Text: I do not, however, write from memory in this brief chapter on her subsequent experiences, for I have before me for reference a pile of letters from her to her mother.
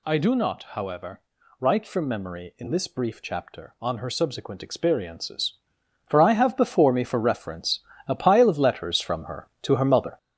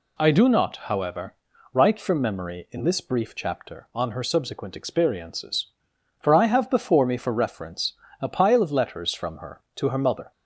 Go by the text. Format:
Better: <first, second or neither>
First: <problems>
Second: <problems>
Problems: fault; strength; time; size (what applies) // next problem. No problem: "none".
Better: second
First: gets louder; noticeable; throughout; 6 dB // pauses between "reference" and "a"; slight; at 7.7 s; 0.26 s long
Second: pauses between "reference" and "a"; slight; at 7.9 s; 0.26 s long